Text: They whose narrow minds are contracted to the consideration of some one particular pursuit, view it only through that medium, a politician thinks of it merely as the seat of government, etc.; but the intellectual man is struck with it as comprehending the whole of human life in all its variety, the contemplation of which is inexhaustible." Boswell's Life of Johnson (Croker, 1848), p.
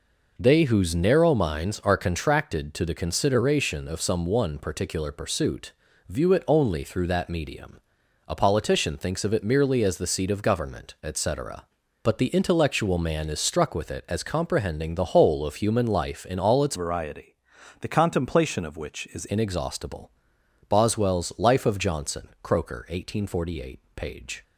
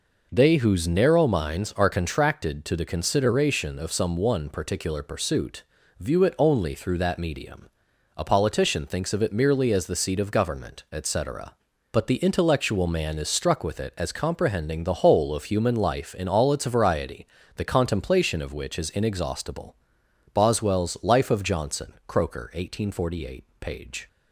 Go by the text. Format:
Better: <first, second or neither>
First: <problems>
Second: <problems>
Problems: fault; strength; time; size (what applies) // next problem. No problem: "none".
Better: second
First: changes voice from "variety" to "is"; from 16.7 to 19.2 s; 2.5 s long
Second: none